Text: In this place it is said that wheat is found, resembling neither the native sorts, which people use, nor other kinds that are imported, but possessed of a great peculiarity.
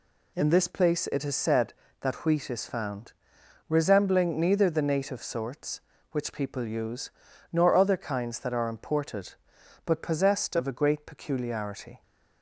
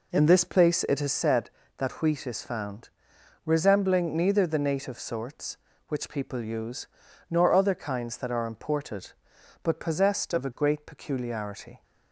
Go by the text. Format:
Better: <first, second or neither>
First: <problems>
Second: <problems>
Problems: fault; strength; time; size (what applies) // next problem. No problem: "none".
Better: first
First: none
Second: starts louder than the rest; until 1.2 s; 4 dB